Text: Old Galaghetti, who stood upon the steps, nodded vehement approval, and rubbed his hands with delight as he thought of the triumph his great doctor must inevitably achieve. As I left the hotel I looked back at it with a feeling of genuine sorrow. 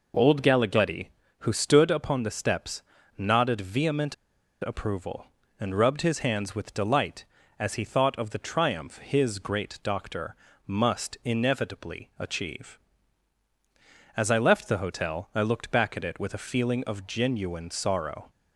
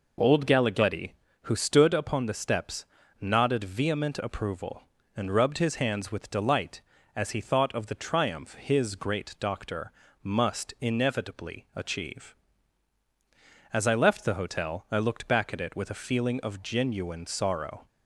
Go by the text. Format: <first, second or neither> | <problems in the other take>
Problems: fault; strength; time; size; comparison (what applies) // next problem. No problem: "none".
second | pauses between "vehement" and "approval"; noticeable; at 4.1 s; 0.47 s long // pauses between "doctor" and "must"; slight; at 10.3 s; 0.32 s long; slight in the second